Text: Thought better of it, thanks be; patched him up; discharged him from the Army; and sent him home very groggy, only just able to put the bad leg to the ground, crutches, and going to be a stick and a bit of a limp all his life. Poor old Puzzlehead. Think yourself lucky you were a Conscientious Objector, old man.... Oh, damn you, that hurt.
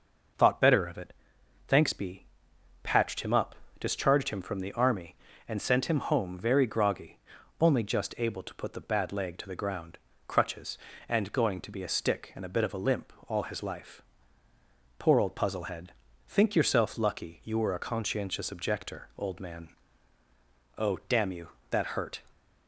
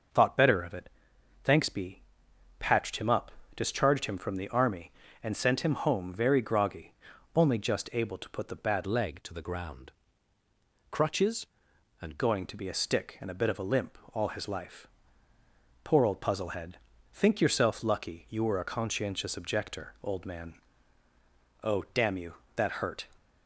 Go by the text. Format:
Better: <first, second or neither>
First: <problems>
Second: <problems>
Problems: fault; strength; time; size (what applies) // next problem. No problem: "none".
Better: first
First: pauses between "limp" and "all"; slight; at 13.1 s; 0.16 s long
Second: changes voice from "leg" to "and"; from 8.8 to 12.1 s; 3.3 s long // pauses between "limp" and "all"; slight; at 13.9 s; 0.16 s long